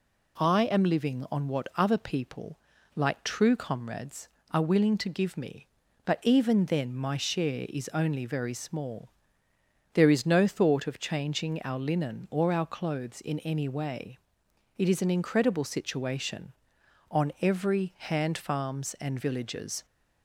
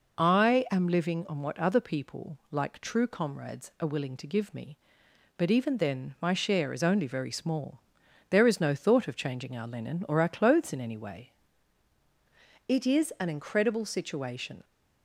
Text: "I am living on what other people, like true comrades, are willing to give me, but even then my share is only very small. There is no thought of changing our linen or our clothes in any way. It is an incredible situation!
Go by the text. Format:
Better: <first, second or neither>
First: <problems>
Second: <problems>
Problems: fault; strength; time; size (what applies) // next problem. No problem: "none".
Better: second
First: goes on to say "On every hand farms and villages"; strong; from 17.1 s on; 2.7 s long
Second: none